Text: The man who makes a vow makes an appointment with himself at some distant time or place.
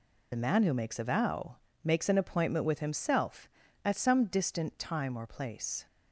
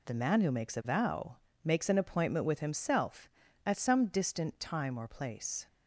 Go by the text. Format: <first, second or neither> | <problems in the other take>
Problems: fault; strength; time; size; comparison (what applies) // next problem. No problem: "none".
second | loses the start of "The"; at 0.3 s; 35 ms // pauses between "vow" and "makes"; slight; at 1.5 s; 0.30 s long; slight in the second